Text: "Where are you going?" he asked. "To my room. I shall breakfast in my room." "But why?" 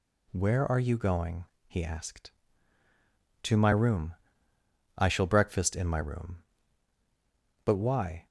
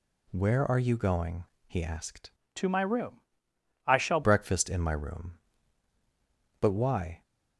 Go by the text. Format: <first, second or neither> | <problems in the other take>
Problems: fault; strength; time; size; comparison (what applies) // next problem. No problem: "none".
first | changes voice from "To" to "shall"; from 2.5 to 4.2 s; 1.7 s long